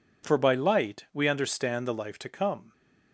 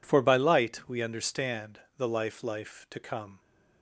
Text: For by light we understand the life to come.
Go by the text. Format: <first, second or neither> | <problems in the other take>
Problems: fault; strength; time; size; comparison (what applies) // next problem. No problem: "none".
first | pauses between "understand" and "the"; slight; at 1.7 s; 0.16 s long // says "life" twice; at 2.4 s